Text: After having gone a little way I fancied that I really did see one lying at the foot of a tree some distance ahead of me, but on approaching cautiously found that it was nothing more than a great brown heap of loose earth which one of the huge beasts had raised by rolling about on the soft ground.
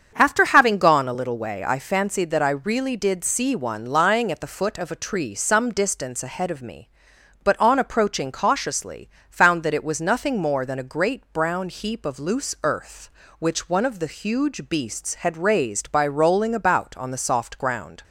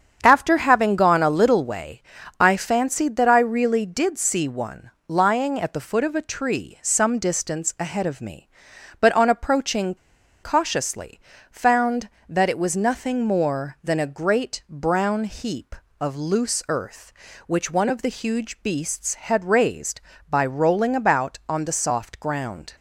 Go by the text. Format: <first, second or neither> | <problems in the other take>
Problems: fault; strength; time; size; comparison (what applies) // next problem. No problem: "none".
first | starts louder than the rest; strong; until 1.2 s; 7.5 dB; strong in the first // pauses between "way" and "I"; slight; at 2.0 s; 0.36 s long // pauses between "one" and "lying"; slight; at 4.9 s; 0.16 s long // pauses between "approaching" and "cautiously"; noticeable; at 9.9 s; 0.48 s long // pauses between "cautiously" and "found"; slight; at 11.2 s; 0.32 s long; slight in the first